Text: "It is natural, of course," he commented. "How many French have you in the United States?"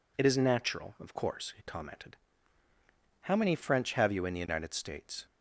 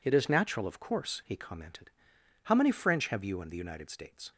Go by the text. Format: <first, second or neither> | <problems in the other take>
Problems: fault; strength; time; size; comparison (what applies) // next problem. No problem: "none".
neither | none